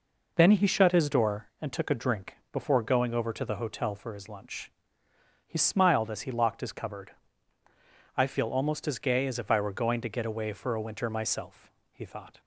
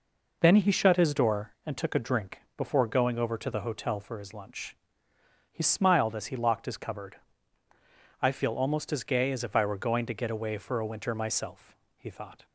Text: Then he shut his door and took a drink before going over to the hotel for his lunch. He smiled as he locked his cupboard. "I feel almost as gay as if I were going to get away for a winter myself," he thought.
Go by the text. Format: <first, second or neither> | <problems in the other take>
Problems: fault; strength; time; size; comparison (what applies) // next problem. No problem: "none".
neither | pauses between "drink" and "before"; slight; the same in both